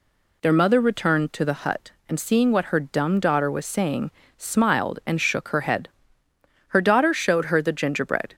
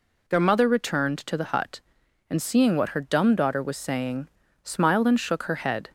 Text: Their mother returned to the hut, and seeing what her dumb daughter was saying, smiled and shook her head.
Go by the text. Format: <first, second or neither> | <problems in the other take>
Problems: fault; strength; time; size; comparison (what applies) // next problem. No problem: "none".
second | goes on to say "Her daughter showed her the gingerbread"; from 6.6 s on; 1.6 s long